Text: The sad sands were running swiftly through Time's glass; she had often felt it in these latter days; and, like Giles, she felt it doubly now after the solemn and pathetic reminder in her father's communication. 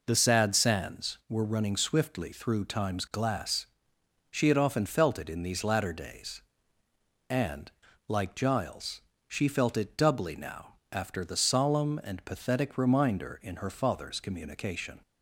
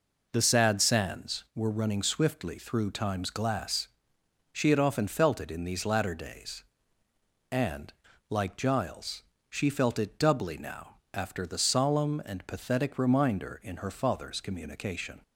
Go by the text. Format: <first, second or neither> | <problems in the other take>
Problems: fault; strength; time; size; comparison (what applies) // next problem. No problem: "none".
neither | pauses between "now" and "after"; slight; the same in both